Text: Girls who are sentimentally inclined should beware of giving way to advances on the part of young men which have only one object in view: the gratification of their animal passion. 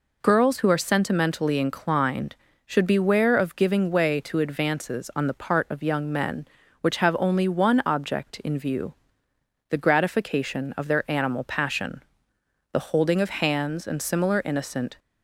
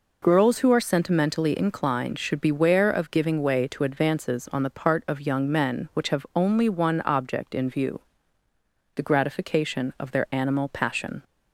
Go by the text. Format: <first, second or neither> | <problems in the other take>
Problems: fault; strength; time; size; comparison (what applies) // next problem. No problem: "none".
second | goes on to say "The holding of hands and similar innocent"; strong; from 12.7 s on; 2.2 s long